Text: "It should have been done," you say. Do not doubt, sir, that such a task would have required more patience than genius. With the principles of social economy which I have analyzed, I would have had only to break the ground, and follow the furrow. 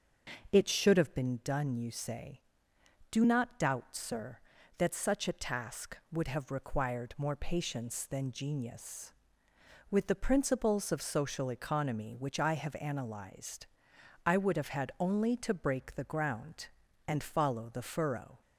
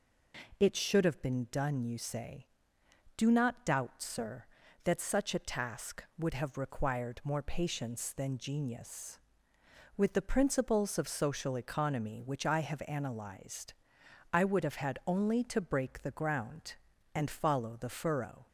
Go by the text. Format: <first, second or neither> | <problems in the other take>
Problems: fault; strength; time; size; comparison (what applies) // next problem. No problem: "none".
second | starts louder than the rest; until 1.3 s; 6.5 dB